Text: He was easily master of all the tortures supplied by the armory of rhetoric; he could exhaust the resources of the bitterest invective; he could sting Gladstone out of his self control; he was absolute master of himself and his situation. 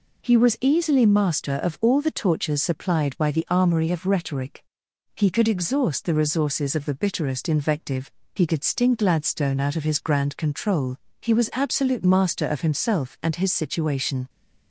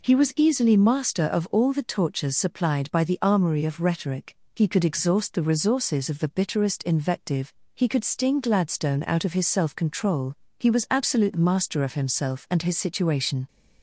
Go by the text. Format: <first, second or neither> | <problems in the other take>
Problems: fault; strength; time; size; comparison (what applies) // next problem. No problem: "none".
second | says "grand" for "self"; at 9.9 s